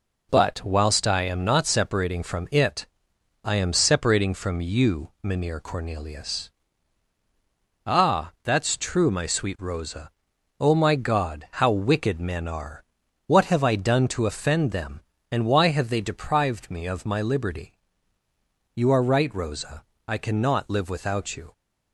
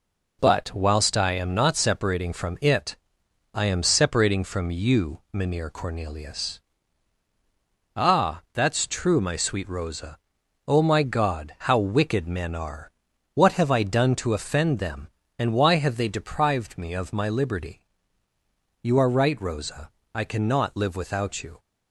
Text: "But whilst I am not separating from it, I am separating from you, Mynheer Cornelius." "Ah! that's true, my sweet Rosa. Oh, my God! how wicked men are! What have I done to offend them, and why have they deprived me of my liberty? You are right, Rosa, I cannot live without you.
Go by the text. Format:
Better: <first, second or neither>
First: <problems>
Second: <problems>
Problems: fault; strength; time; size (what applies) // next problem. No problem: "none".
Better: neither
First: none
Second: none